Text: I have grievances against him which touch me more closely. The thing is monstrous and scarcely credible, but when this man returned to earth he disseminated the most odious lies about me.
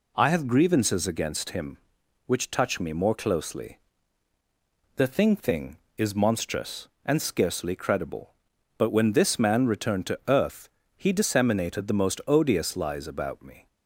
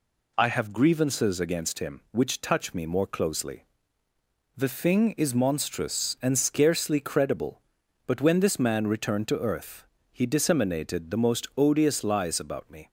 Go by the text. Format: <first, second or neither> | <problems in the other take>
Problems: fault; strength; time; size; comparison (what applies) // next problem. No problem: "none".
second | says "thing" twice; at 5.3 s // pauses between "earth" and "he"; slight; at 10.6 s; 0.28 s long; slight in the second